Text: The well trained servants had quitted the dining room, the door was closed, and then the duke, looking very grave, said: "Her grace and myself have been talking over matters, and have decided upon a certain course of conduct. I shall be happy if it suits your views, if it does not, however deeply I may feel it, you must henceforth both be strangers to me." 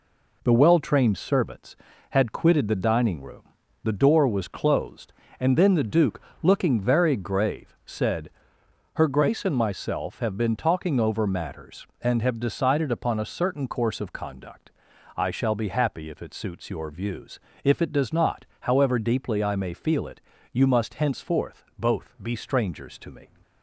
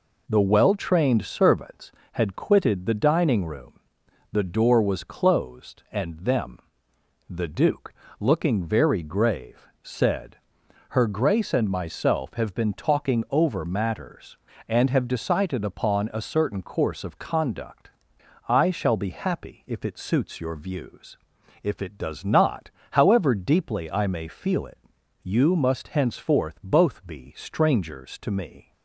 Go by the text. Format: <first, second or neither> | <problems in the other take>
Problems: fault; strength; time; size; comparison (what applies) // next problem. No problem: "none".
first | says "them" for "then"; at 6.1 s